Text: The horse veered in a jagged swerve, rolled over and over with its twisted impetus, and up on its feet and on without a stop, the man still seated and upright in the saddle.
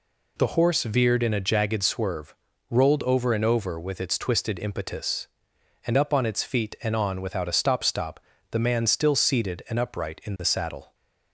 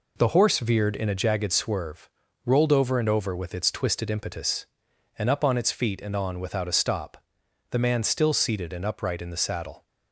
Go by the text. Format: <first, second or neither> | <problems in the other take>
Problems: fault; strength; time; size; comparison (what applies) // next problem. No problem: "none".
second | says "stop" twice; at 7.8 s